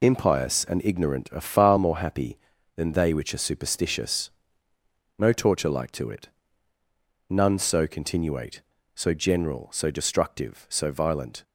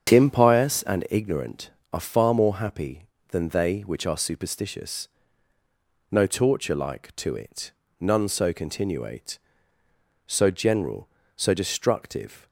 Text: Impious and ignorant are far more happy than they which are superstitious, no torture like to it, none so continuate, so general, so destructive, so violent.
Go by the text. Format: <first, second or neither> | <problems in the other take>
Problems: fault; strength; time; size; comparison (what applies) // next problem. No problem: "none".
first | starts louder than the rest; strong; until 1.1 s; 7.5 dB // stops before "so violent"; at 12.4 s